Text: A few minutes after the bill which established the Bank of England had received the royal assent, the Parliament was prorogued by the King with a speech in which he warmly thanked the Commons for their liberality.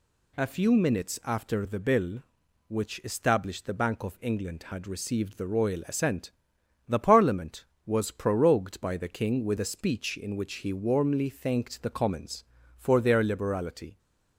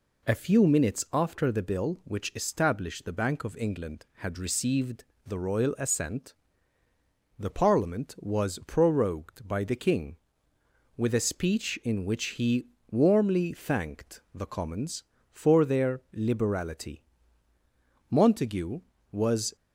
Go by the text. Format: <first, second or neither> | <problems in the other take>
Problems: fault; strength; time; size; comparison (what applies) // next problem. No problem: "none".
first | pauses between "received" and "the"; slight; at 5.0 s; 0.22 s long // pauses between "he" and "warmly"; slight; at 12.6 s; 0.24 s long // goes on to say "Montague was"; from 18.1 s on; 1.4 s long